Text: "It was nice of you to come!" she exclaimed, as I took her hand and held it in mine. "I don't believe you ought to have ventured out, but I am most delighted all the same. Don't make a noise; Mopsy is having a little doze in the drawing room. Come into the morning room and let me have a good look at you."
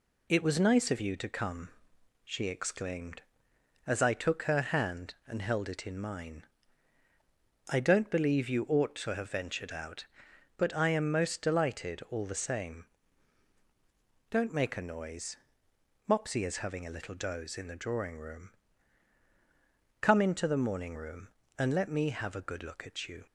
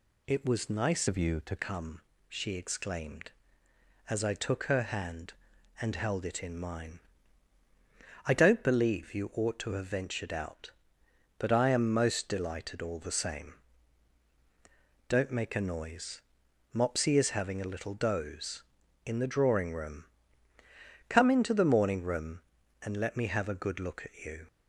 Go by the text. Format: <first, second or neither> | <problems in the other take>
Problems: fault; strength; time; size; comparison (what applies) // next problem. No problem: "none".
first | changes voice from "of" to "to"; from 1.0 to 1.5 s; 0.5 s long